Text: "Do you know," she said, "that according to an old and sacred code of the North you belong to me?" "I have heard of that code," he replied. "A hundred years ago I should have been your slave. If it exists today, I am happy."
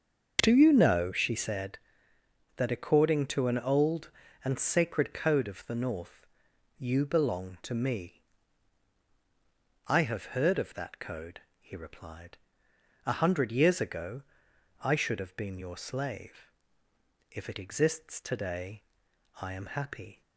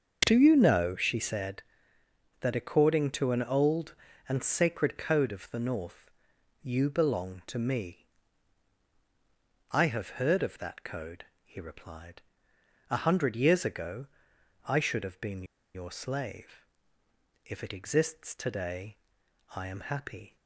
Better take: first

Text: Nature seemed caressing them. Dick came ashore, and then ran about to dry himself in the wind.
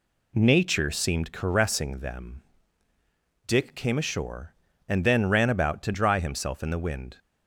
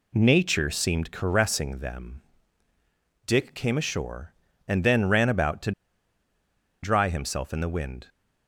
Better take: first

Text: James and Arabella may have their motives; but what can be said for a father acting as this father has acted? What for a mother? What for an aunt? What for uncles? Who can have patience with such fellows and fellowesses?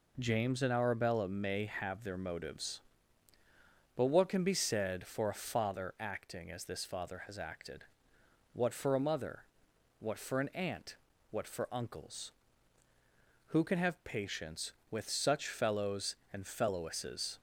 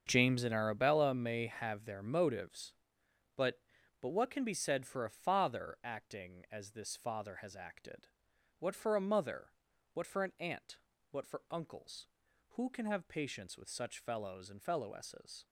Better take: first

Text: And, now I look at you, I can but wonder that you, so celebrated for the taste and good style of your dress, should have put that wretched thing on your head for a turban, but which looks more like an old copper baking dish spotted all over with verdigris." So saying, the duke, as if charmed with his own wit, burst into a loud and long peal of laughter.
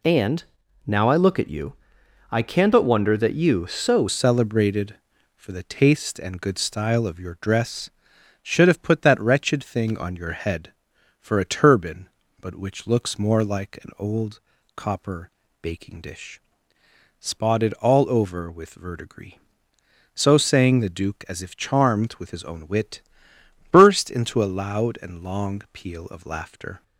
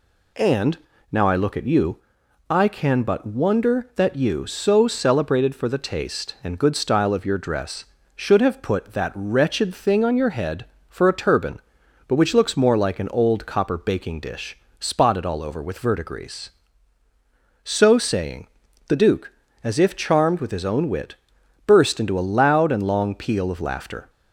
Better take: second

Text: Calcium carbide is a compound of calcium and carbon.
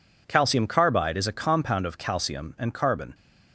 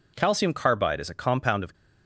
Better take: first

